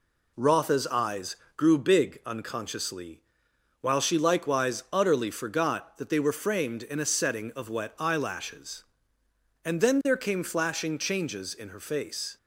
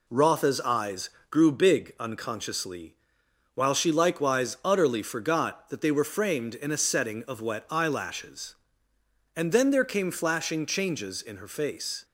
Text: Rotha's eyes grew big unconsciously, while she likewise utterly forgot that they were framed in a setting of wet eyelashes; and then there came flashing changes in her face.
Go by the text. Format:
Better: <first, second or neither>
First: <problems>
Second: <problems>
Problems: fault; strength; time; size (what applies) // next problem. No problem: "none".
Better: neither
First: pauses between "eyes" and "grew"; slight; at 1.3 s; 0.22 s long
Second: pauses between "eyes" and "grew"; slight; at 1.0 s; 0.22 s long